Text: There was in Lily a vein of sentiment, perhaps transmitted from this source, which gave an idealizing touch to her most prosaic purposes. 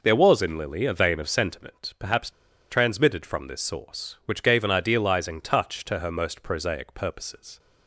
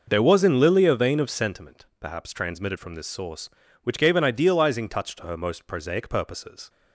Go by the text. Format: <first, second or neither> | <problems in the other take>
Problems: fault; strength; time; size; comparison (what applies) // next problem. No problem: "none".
second | pauses between "perhaps" and "transmitted"; at 2.3 s; 0.38 s long